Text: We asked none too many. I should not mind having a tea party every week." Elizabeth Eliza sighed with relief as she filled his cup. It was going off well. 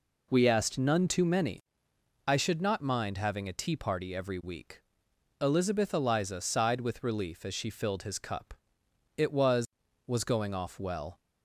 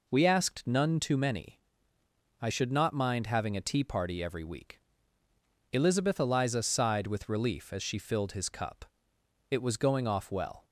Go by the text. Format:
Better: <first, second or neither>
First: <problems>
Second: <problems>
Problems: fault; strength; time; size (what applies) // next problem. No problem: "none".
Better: second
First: says "was" twice; at 10.0 s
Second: none